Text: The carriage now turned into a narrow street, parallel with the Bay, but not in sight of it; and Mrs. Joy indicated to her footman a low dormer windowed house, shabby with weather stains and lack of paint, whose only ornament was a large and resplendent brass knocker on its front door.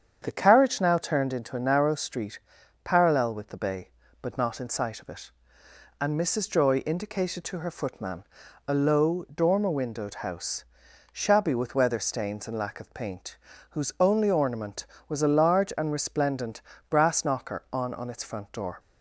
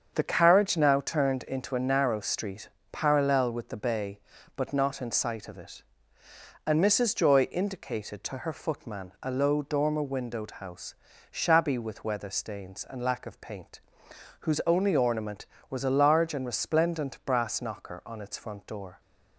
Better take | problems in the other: second | starts louder than the rest; strong; until 1.2 s; 8 dB; strong in the second // pauses between "footman" and "a"; at 8.2 s; 0.42 s long // pauses between "resplendent" and "brass"; slight; at 16.6 s; 0.28 s long // says "on" twice; at 17.9 s

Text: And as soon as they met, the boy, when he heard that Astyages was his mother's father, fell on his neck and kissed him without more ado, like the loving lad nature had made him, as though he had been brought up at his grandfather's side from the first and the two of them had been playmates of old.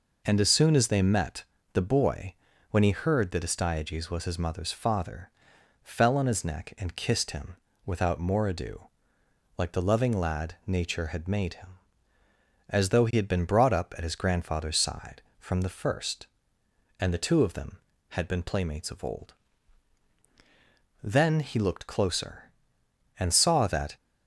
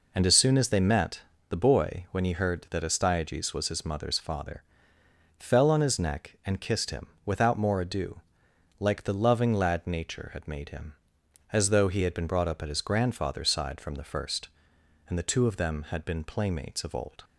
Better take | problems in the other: second | pauses between "him" and "without"; slight; at 7.5 s; 0.30 s long; slight in the second // goes on to say "Then he looked closer and saw that"; strong; from 21.0 s on; 2.9 s long

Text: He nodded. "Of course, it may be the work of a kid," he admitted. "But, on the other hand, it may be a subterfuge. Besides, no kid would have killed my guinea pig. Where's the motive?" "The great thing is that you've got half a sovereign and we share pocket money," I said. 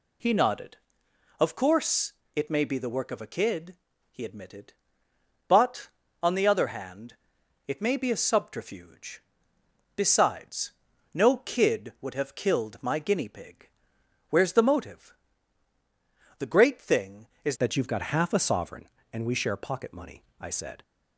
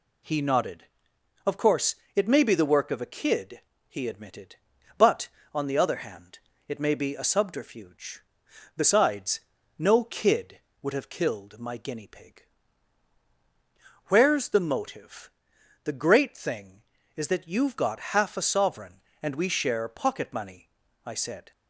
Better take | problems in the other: second | changes voice at "that"; from 17.5 s on; 3.3 s long

